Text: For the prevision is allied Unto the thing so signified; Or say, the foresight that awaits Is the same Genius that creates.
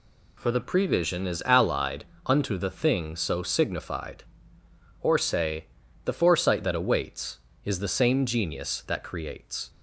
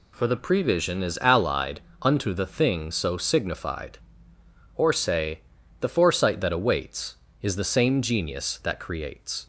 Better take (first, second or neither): neither